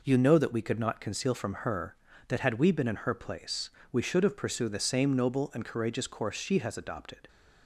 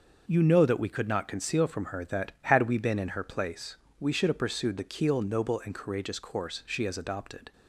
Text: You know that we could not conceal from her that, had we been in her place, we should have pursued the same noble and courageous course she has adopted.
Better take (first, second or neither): first